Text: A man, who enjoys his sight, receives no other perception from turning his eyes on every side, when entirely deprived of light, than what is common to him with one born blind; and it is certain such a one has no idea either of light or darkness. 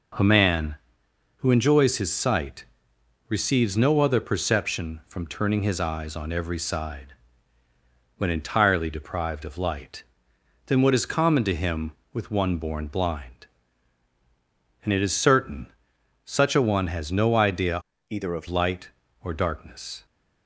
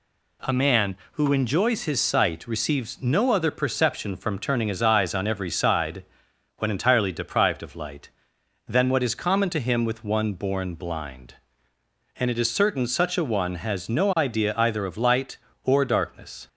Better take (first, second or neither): second